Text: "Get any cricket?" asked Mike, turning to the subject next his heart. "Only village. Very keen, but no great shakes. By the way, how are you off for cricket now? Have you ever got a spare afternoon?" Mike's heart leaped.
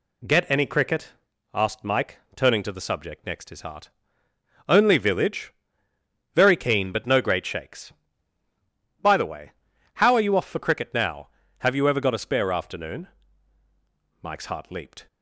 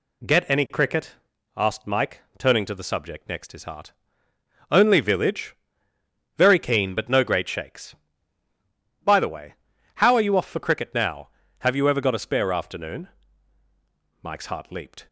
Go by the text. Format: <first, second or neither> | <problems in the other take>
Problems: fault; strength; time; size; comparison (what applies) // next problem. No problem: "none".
neither | none